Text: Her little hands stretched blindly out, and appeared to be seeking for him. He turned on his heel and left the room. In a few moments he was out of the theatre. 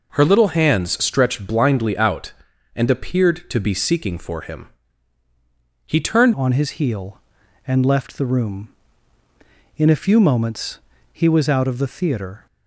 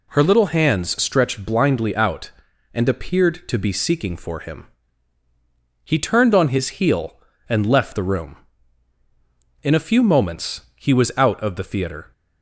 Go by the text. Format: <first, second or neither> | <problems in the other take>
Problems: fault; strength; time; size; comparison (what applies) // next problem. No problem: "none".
second | changes voice at "on"; from 6.3 s on; 6.1 s long // pauses between "moments" and "he"; slight; at 10.8 s; 0.32 s long